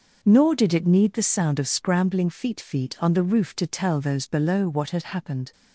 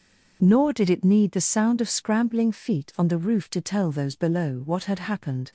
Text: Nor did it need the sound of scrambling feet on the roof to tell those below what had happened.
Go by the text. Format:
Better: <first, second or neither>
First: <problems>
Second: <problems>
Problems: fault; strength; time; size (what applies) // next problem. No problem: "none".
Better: second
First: says "feet" twice; at 2.5 s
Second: none